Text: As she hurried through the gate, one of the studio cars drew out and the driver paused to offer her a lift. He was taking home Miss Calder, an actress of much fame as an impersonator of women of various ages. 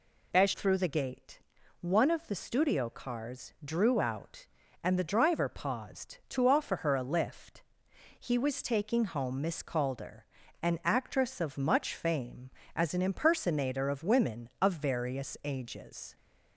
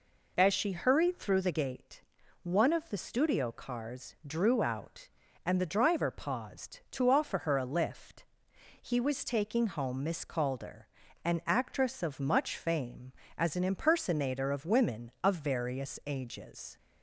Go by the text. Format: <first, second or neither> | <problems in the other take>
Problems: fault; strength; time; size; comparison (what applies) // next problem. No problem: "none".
second | skips "she hurried"; at 0.5 s